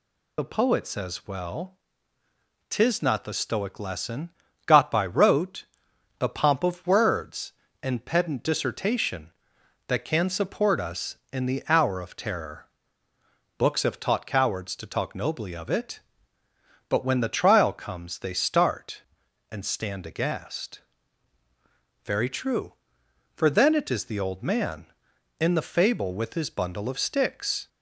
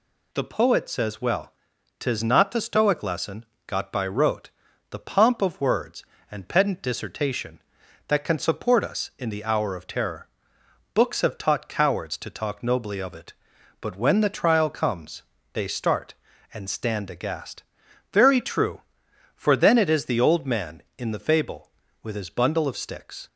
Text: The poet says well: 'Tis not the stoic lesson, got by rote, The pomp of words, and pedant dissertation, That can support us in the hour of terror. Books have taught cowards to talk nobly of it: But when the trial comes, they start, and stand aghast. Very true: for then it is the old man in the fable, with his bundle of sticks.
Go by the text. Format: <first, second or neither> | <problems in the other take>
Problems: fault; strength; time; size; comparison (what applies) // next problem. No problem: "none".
second | loses the start of "The"; at 0.3 s; 45 ms